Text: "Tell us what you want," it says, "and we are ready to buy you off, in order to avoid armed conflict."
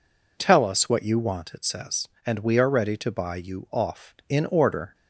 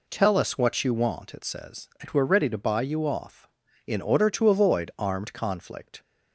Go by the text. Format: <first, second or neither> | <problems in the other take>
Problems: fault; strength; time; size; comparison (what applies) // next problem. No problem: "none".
second | stops before "to avoid armed conflict"; at 4.9 s